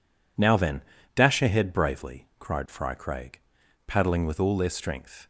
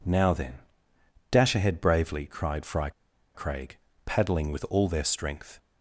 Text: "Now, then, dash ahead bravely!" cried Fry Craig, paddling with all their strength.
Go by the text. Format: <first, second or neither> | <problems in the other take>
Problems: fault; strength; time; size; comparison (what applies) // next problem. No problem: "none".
first | pauses between "Fry" and "Craig"; at 2.8 s; 0.44 s long